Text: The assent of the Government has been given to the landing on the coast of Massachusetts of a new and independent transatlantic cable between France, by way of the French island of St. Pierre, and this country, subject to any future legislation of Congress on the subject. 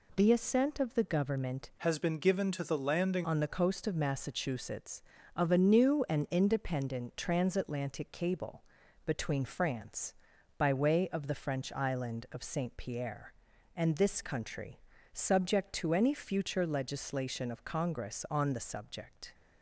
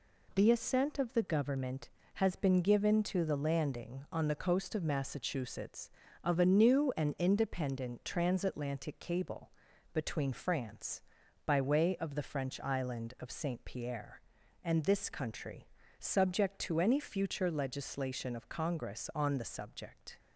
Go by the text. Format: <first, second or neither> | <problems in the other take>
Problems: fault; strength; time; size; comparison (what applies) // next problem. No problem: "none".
second | changes voice from "has" to "landing"; from 1.7 to 3.2 s; 1.5 s long // pauses between "cable" and "between"; at 8.6 s; 0.42 s long; also in the second